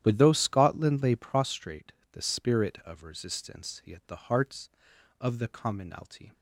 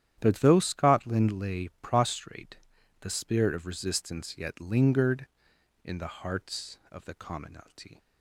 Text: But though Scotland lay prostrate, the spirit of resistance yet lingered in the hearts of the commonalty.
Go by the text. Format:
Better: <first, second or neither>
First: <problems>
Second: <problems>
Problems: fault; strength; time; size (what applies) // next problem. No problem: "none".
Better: second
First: starts louder than the rest; strong; until 1.0 s; 11 dB // skips "lingered in"; at 4.0 s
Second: starts louder than the rest; strong; until 1.1 s; 10.5 dB